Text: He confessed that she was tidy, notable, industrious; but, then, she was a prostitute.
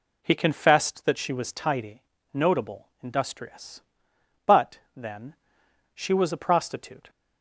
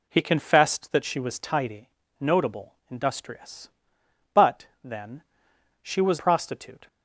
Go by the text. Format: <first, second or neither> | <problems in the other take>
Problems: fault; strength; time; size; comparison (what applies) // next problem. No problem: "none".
first | skips "a"; at 6.1 s